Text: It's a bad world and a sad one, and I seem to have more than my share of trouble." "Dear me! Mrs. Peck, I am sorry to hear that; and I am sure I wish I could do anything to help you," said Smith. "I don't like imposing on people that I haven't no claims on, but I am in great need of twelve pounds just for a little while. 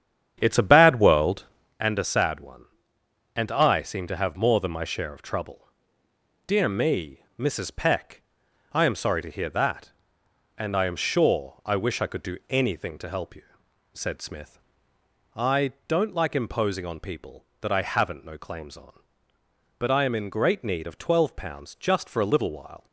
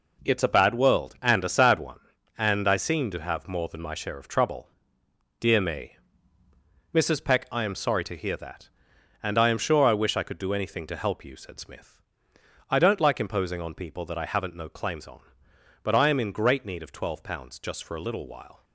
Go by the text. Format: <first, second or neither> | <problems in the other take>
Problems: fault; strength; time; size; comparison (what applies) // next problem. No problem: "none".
second | starts louder than the rest; strong; until 1.8 s; 9 dB // pauses between "I" and "don't"; slight; at 15.7 s; 0.16 s long